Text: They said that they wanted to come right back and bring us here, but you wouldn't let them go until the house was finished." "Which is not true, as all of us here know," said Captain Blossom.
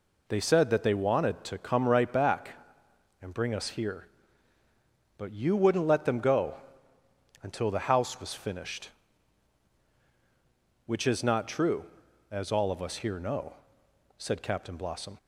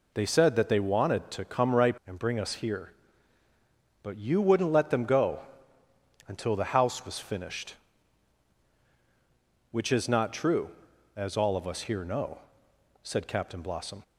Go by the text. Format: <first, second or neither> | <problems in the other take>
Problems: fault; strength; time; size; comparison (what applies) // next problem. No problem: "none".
first | skips "back"; at 2.0 s // pauses between "go" and "until"; noticeable; at 5.4 s; 0.86 s long; noticeable in the first